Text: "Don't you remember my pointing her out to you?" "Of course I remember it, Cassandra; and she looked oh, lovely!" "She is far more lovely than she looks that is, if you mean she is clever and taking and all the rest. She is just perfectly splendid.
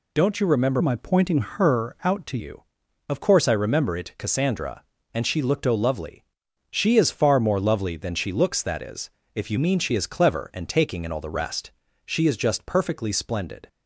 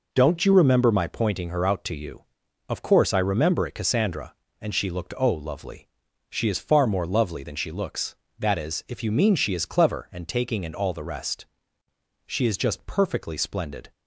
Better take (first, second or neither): second